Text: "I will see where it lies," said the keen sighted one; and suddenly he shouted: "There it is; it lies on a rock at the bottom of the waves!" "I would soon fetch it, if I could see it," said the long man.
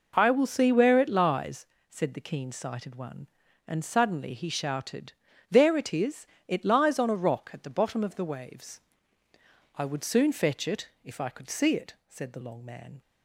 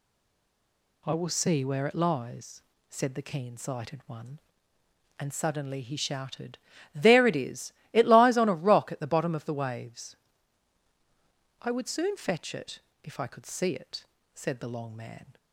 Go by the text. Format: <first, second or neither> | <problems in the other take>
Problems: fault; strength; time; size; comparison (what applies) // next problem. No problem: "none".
first | stays silent before the first word; until 1.0 s; 1.0 s long